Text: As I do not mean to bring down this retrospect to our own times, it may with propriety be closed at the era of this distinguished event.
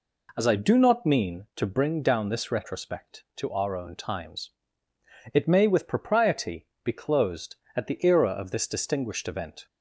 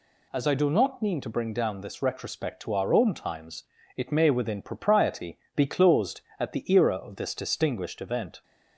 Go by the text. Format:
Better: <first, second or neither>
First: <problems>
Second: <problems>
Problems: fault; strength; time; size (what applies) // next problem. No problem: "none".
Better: first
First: pauses between "propriety" and "be"; slight; at 6.6 s; 0.18 s long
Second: says "within" for "with"; at 4.2 s // pauses between "propriety" and "be"; slight; at 5.3 s; 0.18 s long